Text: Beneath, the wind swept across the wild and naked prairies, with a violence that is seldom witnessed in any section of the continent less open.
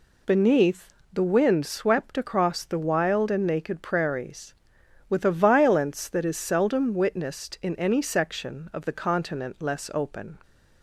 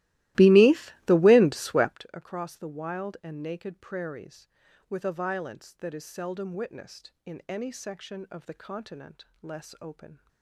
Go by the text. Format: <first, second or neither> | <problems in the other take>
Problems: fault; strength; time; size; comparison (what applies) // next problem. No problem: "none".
first | starts louder than the rest; strong; until 2.1 s; 17.5 dB // pauses between "continent" and "less"; slight; at 9.2 s; 0.18 s long